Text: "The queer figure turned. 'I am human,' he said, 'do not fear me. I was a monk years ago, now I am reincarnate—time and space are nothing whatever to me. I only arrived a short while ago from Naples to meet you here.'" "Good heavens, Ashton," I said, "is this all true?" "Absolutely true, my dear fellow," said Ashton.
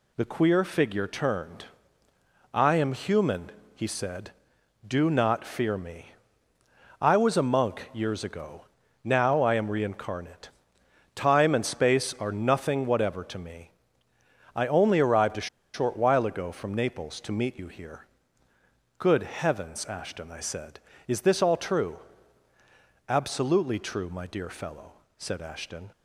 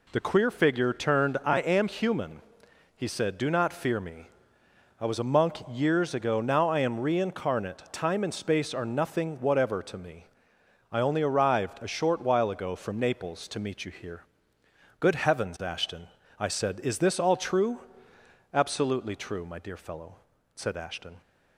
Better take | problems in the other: second | pauses between "a" and "short"; slight; at 15.4 s; 0.27 s long

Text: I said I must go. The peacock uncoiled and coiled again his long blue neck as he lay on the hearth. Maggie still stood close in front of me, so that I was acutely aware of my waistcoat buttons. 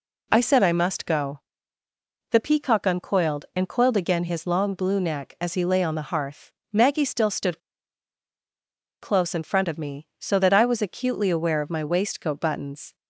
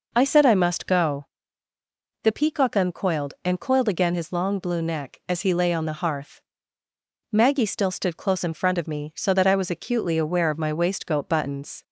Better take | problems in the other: second | pauses between "stood" and "close"; strong; at 7.6 s; 1.4 s long

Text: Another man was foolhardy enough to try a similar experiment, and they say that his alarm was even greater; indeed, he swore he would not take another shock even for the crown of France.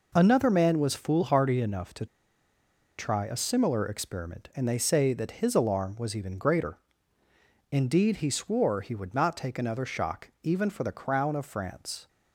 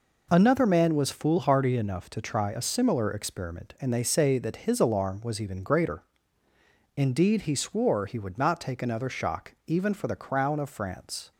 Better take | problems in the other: second | pauses between "to" and "try"; noticeable; at 2.0 s; 0.92 s long

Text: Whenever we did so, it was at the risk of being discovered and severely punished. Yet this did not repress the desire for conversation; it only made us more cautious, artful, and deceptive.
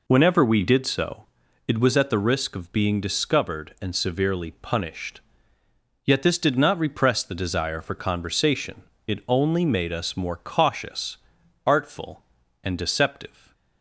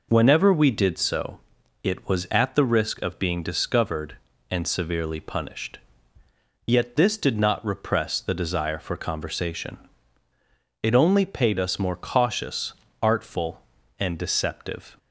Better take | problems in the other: first | says "paid" for "made"; at 11.2 s

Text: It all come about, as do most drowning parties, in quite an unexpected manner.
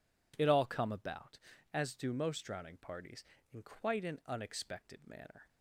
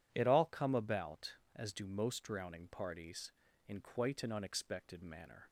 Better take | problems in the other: neither | none

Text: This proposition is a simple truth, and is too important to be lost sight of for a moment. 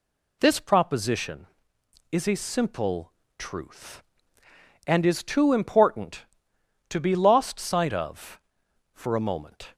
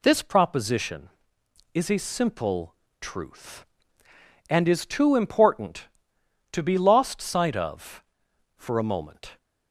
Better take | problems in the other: neither | pauses between "simple" and "truth"; slight; the same in both

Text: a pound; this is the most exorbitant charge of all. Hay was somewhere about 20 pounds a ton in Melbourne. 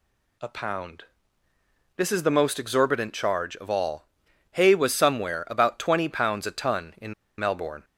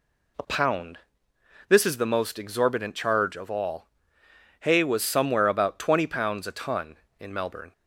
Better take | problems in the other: second | pauses between "in" and "Melbourne"; slight; at 7.1 s; 0.24 s long

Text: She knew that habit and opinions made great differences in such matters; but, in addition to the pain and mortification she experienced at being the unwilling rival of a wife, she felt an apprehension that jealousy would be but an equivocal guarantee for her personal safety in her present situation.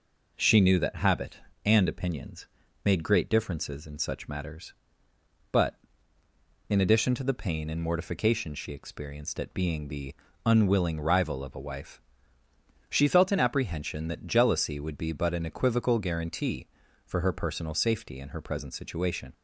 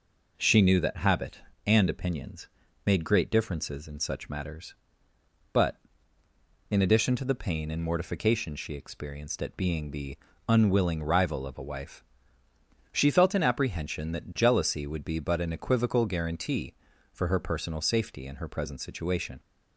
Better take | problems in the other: neither | pauses between "opinions" and "made"; the same in both // pauses between "the" and "unwilling"; slight; the same in both

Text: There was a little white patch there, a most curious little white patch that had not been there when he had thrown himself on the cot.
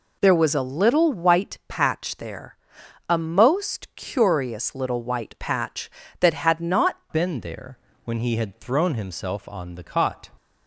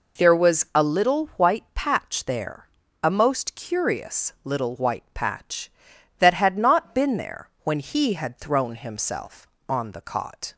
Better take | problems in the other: second | changes voice at "been"; from 7.1 s on; 3.1 s long // pauses between "there" and "when"; slight; at 7.7 s; 0.26 s long

